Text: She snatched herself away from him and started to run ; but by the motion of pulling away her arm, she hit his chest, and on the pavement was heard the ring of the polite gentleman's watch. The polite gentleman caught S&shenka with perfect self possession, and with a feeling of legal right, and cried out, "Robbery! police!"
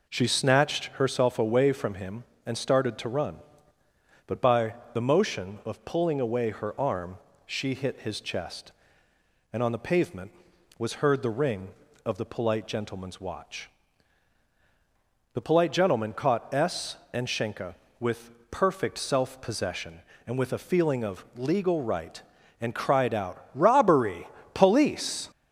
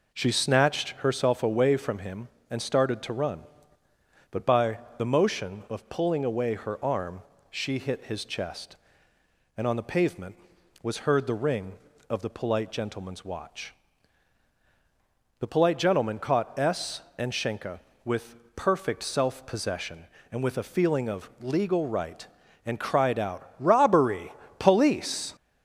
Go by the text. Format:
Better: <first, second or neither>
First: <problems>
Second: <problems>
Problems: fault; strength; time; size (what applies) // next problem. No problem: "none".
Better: neither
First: pauses between "by" and "the"; slight; at 4.7 s; 0.18 s long // pauses between "with" and "perfect"; slight; at 18.3 s; 0.20 s long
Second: pauses between "by" and "the"; slight; at 4.7 s; 0.18 s long // pauses between "with" and "perfect"; slight; at 18.3 s; 0.20 s long